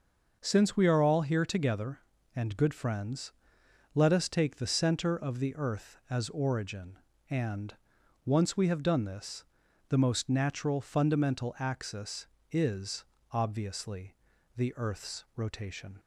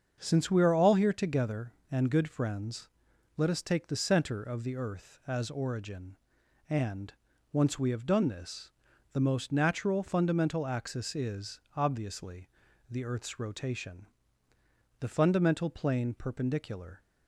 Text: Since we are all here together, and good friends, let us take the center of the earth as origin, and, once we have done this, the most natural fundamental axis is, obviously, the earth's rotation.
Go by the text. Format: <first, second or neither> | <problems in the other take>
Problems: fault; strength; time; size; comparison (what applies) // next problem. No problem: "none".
first | starts louder than the rest; until 1.2 s; 7 dB; noticeable in the first // goes on to say "The fundamental plane perpendicular"; strong; from 14.9 s on; 2.0 s long